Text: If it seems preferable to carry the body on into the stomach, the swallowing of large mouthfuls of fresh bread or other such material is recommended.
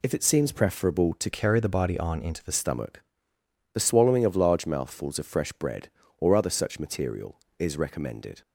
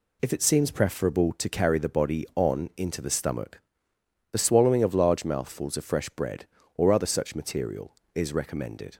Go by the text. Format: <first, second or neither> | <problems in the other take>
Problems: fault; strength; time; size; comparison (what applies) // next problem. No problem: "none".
second | changes voice from "carry" to "the"; from 1.3 to 2.5 s; 1.2 s long